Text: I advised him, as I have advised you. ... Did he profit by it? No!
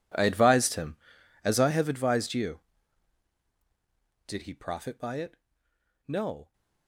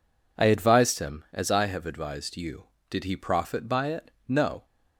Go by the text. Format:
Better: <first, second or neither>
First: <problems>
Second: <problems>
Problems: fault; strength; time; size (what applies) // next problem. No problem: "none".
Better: second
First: gets quieter; strong; throughout; 21 dB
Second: none